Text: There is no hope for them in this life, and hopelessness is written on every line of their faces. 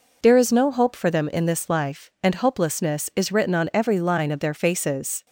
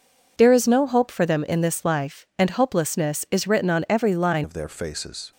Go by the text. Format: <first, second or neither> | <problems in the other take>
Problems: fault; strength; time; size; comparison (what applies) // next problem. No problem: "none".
first | changes voice at "of"; from 4.4 s on; 0.9 s long